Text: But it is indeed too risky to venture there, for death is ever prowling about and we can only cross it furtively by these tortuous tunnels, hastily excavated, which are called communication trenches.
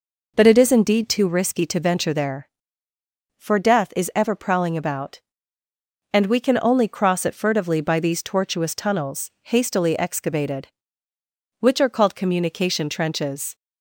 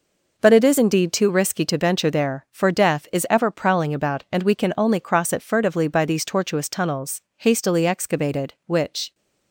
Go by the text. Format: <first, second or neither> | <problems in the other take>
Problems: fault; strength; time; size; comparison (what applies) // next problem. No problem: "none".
first | stops before "are called communication trenches"; at 9.1 s